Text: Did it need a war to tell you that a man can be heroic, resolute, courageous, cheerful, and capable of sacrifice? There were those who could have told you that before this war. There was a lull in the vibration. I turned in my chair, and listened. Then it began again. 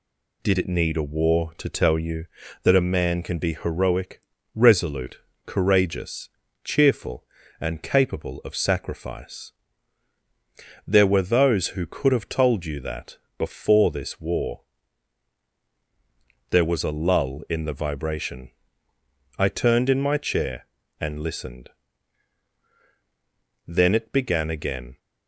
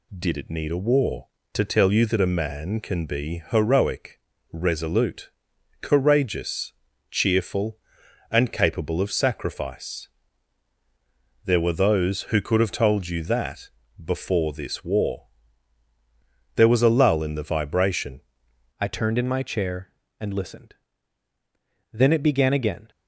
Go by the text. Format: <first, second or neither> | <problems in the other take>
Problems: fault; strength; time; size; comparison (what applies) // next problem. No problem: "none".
first | pauses between "that" and "before"; slight; at 13.6 s; 0.36 s long; slight in the first // changes voice at "I"; from 18.8 s on; 4.1 s long